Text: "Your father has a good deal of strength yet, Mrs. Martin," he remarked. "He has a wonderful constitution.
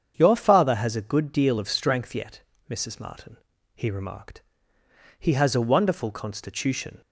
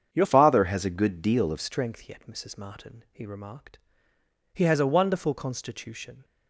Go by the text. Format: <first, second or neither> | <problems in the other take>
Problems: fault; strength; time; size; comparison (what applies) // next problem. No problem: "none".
first | starts louder than the rest; strong; until 1.1 s; 7.5 dB; strong in the first // changes voice from "father" to "of"; from 0.2 to 1.5 s; 1.3 s long